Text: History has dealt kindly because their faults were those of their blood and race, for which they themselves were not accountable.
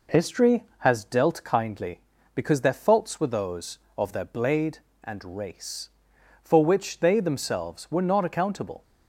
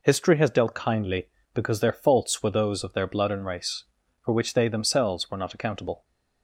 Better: second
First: says "blade" for "blood"; at 4.2 s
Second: none

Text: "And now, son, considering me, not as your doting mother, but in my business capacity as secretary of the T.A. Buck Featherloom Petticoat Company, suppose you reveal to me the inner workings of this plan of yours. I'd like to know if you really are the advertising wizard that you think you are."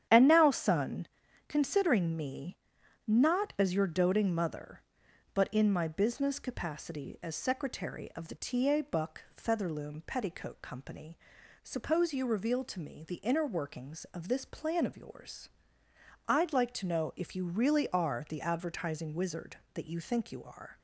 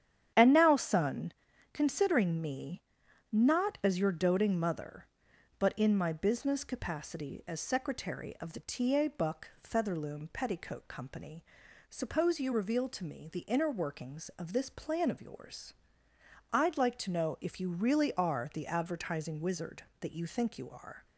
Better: neither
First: starts louder than the rest; strong; until 1.5 s; 9.5 dB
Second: starts louder than the rest; strong; until 1.7 s; 9.5 dB

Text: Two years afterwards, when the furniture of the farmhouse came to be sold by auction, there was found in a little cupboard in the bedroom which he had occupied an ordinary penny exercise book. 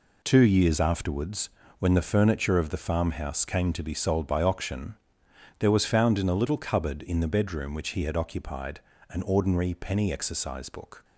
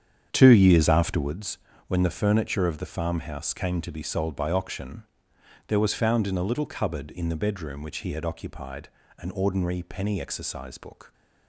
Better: first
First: pauses between "occupied" and "an"; slight; at 8.7 s; 0.30 s long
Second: starts louder than the rest; strong; until 1.3 s; 8.5 dB // pauses between "occupied" and "an"; slight; at 8.8 s; 0.30 s long

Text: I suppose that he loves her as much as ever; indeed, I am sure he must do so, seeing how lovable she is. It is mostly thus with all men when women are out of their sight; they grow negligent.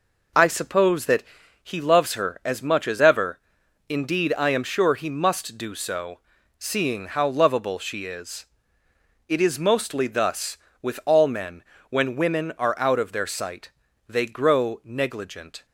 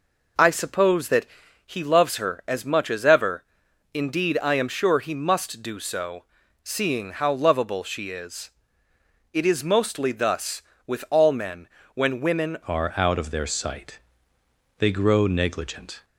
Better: first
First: pauses between "that" and "he"; at 1.2 s; 0.40 s long // pauses between "men" and "when"; slight; at 11.6 s; 0.26 s long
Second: pauses between "that" and "he"; at 1.2 s; 0.40 s long // pauses between "men" and "when"; slight; at 11.6 s; 0.26 s long // changes voice at "are"; from 12.6 s on; 3.4 s long

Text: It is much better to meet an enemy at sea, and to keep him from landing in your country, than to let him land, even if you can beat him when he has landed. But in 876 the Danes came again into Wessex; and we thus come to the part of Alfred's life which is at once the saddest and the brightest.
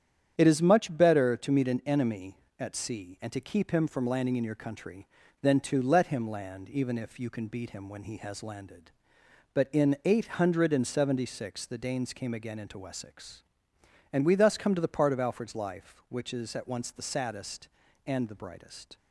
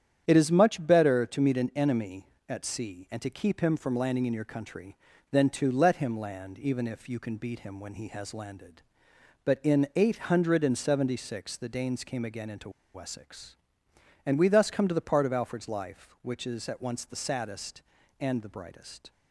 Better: first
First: starts louder than the rest; strong; until 1.3 s; 9 dB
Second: starts louder than the rest; strong; until 1.2 s; 9 dB // pauses between "into" and "Wessex"; slight; at 12.6 s; 0.24 s long

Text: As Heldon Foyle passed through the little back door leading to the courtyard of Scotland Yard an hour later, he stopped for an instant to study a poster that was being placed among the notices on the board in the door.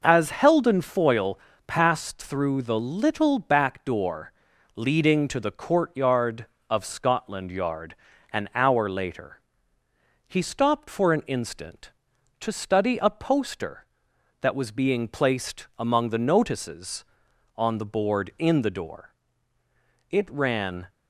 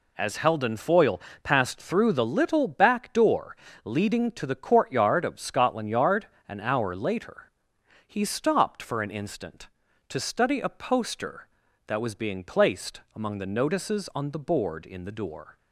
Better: second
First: pauses between "Foyle" and "passed"; slight; at 1.3 s; 0.28 s long // pauses between "door" and "leading"; at 4.3 s; 0.42 s long // pauses between "Yard" and "an"; at 7.9 s; 0.38 s long // goes on to say "It ran"; noticeable; from 20.1 s on; 0.78 s long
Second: pauses between "Foyle" and "passed"; slight; at 1.1 s; 0.24 s long // pauses between "door" and "leading"; slight; at 3.5 s; 0.26 s long // pauses between "Yard" and "an"; slight; at 6.2 s; 0.20 s long

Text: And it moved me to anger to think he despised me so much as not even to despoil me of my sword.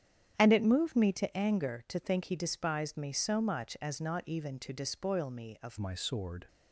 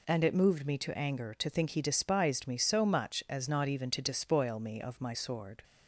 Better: second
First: starts louder than the rest; strong; until 1.3 s; 9 dB // changes voice at "my"; from 5.7 s on; 0.7 s long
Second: none

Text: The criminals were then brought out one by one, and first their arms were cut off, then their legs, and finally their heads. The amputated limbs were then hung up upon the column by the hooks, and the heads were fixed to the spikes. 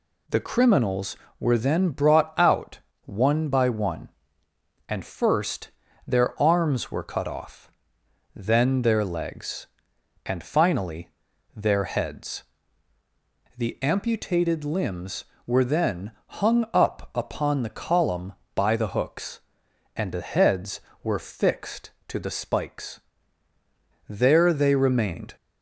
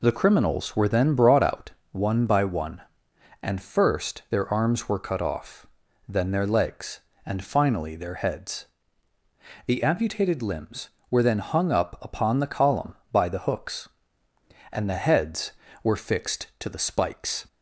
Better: second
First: pauses between "out" and "one"; slight; at 2.8 s; 0.24 s long // pauses between "first" and "their"; slight; at 5.7 s; 0.36 s long // pauses between "finally" and "their"; noticeable; at 11.0 s; 0.46 s long // pauses between "then" and "hung"; slight; at 16.1 s; 0.16 s long // goes on to say "There they remained"; noticeable; from 24.0 s on; 1.2 s long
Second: pauses between "out" and "one"; slight; at 1.6 s; 0.22 s long

